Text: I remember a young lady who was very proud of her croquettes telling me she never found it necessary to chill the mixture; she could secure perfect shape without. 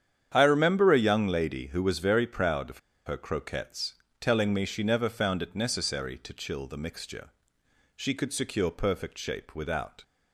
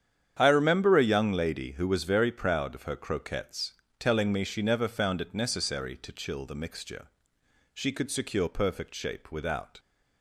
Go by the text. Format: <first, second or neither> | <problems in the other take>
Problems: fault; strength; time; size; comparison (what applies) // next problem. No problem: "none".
second | starts louder than the rest; strong; until 1.3 s; 9 dB; strong in the second // pauses between "of" and "her"; slight; at 2.7 s; 0.27 s long // pauses between "croquettes" and "telling"; slight; at 3.9 s; 0.26 s long; slight in the second